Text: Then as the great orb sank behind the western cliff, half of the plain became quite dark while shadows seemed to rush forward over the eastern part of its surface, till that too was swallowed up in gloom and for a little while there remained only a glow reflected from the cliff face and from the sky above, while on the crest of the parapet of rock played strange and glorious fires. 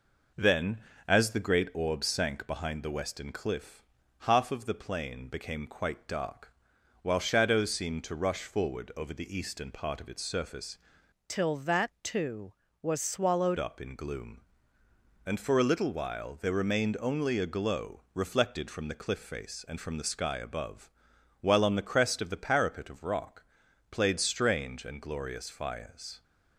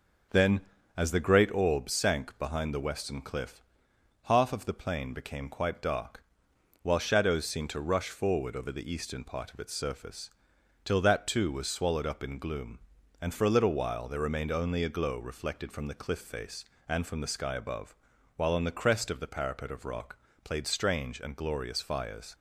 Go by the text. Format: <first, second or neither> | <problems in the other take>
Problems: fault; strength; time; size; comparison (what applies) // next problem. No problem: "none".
second | pauses between "dark" and "while"; noticeable; at 6.4 s; 0.52 s long; noticeable in the second // changes voice from "till" to "swallowed"; from 11.2 to 13.5 s; 2.3 s long // pauses between "rock" and "played"; noticeable; at 23.4 s; 0.46 s long; slight in the second